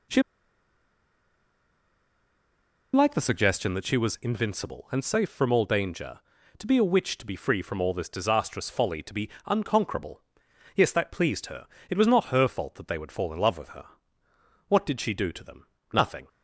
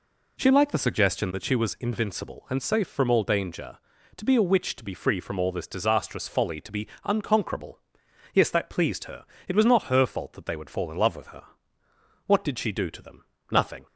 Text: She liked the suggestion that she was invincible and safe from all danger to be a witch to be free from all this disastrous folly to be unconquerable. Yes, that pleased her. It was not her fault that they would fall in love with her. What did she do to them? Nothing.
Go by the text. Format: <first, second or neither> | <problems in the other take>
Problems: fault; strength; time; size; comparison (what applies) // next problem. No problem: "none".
second | pauses between "She" and "liked"; strong; at 0.2 s; 2.7 s long // pauses between "be" and "unconquerable"; slight; at 9.2 s; 0.16 s long; slight in the second